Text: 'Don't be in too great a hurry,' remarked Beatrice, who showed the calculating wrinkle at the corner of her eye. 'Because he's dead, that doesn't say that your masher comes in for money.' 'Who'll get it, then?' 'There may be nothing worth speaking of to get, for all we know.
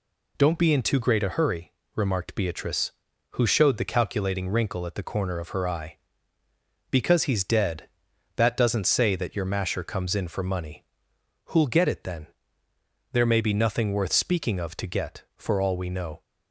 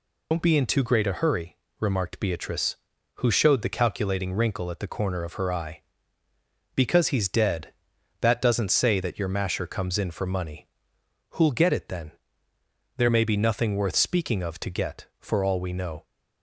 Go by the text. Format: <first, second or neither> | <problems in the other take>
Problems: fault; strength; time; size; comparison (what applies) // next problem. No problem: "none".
first | loses the start of "Don't"; at 0.3 s; 100 ms